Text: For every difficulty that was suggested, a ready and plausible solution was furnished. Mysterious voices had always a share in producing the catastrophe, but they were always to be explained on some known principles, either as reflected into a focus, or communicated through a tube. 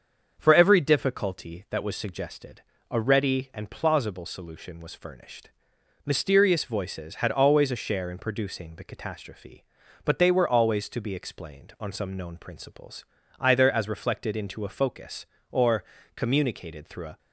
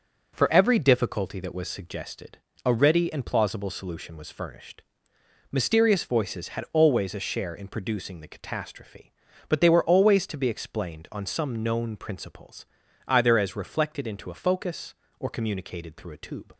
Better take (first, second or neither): second